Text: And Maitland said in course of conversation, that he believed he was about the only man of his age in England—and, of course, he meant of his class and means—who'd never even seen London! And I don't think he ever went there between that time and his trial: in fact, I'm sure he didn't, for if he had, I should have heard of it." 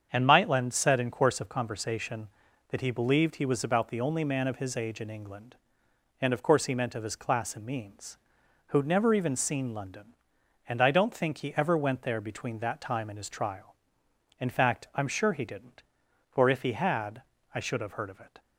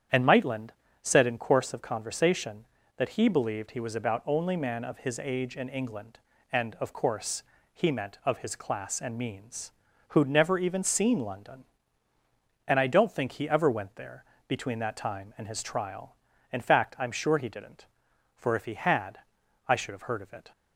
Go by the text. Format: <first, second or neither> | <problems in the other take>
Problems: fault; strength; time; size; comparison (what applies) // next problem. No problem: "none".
first | starts louder than the rest; strong; until 1.4 s; 9 dB; strong in the first // pauses between "Maitland" and "said"; slight; at 0.7 s; 0.30 s long // skips "the"; at 4.2 s // pauses between "there" and "between"; slight; at 14.2 s; 0.24 s long